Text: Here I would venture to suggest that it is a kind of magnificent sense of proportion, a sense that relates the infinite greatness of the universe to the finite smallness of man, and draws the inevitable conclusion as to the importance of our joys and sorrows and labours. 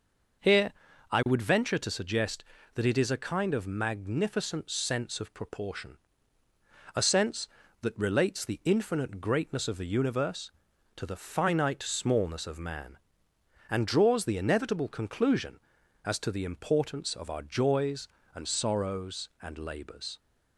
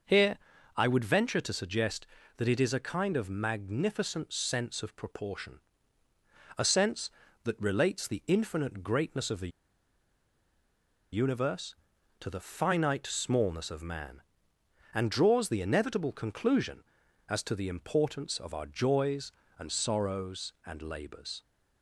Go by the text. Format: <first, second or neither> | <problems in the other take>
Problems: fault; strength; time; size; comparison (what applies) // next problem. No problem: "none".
first | pauses between "Here" and "I"; at 0.3 s; 0.40 s long; also in the first // pauses between "the" and "universe"; strong; at 9.4 s; 1.6 s long